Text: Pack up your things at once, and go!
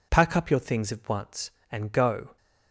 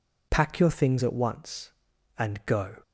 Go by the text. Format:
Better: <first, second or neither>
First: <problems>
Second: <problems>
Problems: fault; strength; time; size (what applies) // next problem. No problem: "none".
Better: first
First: none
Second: skips "up"; at 0.5 s